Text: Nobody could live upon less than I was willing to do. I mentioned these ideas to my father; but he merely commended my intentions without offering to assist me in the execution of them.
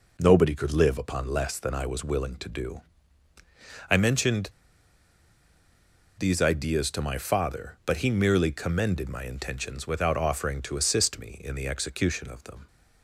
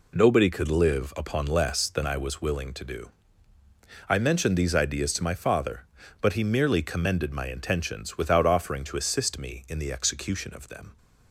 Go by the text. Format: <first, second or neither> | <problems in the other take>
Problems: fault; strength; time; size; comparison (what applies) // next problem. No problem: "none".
second | pauses between "mentioned" and "these"; strong; at 4.4 s; 1.6 s long